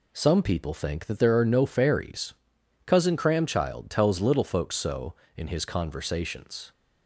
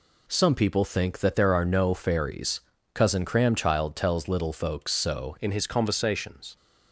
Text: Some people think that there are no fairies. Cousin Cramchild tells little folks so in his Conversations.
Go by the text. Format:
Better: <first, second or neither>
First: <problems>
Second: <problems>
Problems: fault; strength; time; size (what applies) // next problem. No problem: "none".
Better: first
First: none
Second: changes voice at "in"; from 5.4 s on; 1.1 s long